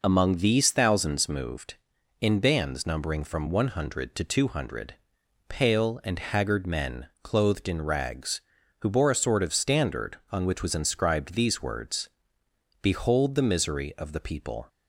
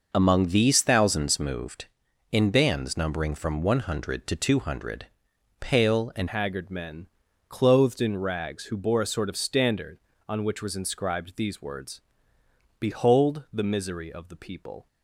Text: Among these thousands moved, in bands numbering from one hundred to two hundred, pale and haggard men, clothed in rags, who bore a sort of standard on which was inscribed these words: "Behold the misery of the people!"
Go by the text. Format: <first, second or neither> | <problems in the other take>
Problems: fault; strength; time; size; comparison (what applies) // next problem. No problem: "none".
first | changes voice at "haggard"; from 6.2 s on; 8.6 s long